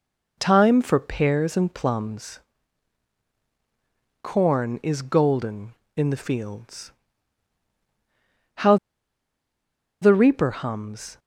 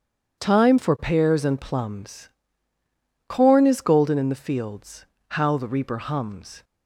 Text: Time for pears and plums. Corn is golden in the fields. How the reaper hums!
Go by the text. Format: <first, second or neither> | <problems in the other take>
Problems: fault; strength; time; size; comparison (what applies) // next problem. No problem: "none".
second | pauses between "How" and "the"; strong; at 8.7 s; 1.2 s long